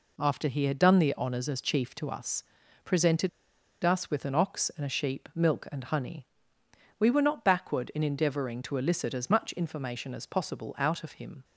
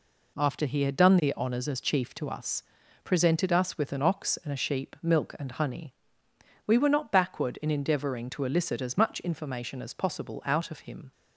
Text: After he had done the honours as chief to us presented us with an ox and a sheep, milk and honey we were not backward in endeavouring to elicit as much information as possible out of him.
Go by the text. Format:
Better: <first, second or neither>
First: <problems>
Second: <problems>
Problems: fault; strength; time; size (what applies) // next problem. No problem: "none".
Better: second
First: pauses between "us" and "presented"; at 2.4 s; 0.40 s long // pauses between "presented" and "us"; noticeable; at 3.2 s; 0.54 s long // pauses between "honey" and "we"; noticeable; at 6.2 s; 0.72 s long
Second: pauses between "us" and "presented"; at 2.6 s; 0.40 s long // pauses between "honey" and "we"; noticeable; at 5.9 s; 0.72 s long